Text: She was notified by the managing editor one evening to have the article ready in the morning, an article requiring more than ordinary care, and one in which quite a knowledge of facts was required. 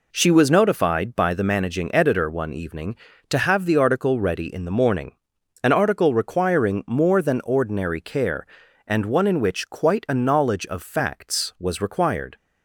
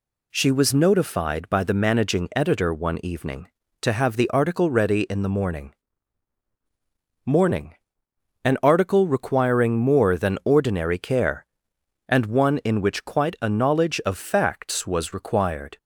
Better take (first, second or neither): first